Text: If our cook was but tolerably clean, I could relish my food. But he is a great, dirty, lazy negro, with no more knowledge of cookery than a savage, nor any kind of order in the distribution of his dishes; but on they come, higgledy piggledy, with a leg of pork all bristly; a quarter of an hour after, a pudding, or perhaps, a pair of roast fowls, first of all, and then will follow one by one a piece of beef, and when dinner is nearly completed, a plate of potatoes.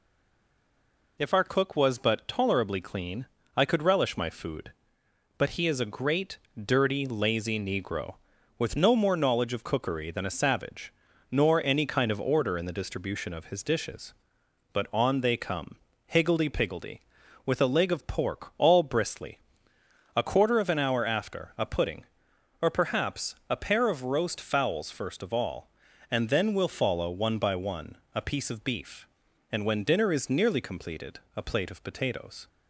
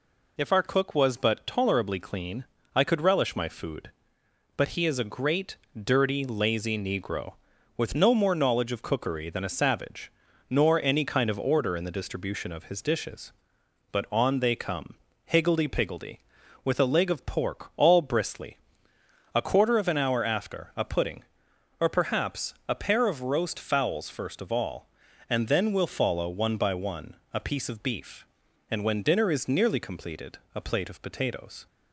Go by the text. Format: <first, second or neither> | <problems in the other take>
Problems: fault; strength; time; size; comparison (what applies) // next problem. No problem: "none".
second | stays silent before the first word; noticeable; until 1.1 s; 1.1 s long // pauses between "one" and "a"; slight; at 27.9 s; 0.18 s long; slight in the second